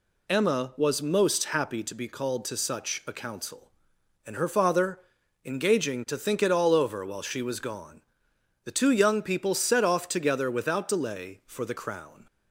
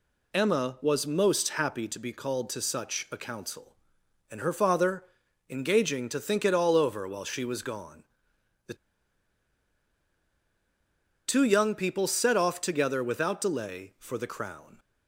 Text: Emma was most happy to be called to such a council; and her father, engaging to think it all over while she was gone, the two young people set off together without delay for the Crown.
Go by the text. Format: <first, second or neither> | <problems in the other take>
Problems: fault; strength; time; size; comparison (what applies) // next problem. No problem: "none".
first | pauses between "the" and "two"; strong; at 8.7 s; 2.5 s long